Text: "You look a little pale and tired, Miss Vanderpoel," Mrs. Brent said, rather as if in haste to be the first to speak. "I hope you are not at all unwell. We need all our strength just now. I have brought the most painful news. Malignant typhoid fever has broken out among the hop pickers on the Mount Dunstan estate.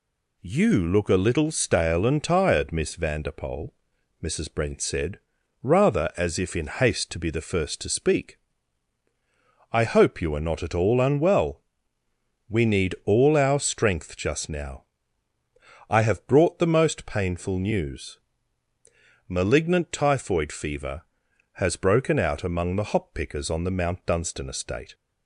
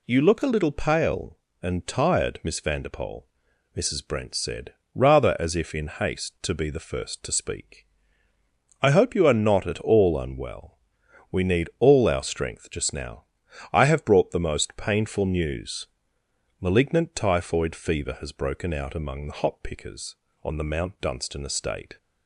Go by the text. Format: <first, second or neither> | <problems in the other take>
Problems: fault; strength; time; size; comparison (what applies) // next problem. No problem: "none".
second | says "stale" for "pale"; at 1.4 s